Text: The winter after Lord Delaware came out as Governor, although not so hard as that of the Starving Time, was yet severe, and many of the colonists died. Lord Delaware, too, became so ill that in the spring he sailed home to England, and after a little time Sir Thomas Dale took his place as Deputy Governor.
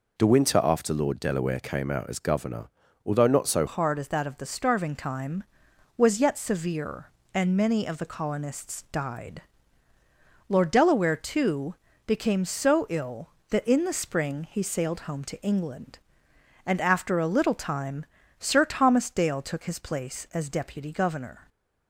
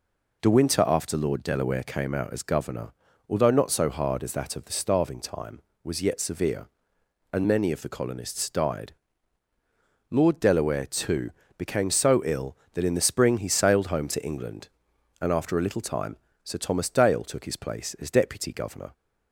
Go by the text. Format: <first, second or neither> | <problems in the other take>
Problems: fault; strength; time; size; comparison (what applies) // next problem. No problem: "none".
second | changes voice at "hard"; from 3.6 s on; 17.8 s long // pauses between "time" and "Sir"; slight; at 18.0 s; 0.34 s long; slight in the second